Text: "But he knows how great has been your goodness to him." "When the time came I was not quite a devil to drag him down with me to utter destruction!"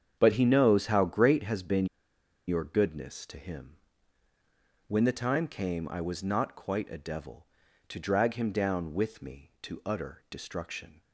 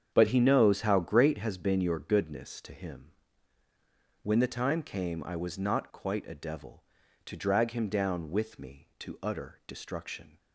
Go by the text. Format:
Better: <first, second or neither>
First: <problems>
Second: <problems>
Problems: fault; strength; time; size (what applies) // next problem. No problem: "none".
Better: second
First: starts louder than the rest; strong; until 1.2 s; 8 dB // pauses between "been" and "your"; noticeable; at 1.8 s; 0.62 s long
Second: starts louder than the rest; strong; until 1.1 s; 7.5 dB